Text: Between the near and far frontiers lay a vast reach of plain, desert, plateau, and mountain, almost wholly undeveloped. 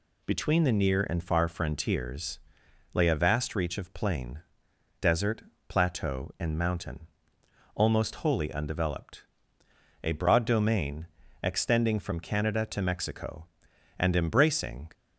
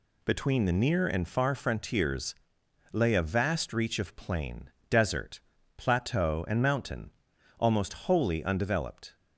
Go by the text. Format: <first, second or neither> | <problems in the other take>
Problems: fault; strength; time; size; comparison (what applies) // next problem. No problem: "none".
second | pauses between "frontiers" and "lay"; noticeable; at 2.3 s; 0.54 s long; noticeable in the second // goes on to say "A broad domain extending from Canada to Mexico and embracing"; strong; from 10.0 s on; 4.9 s long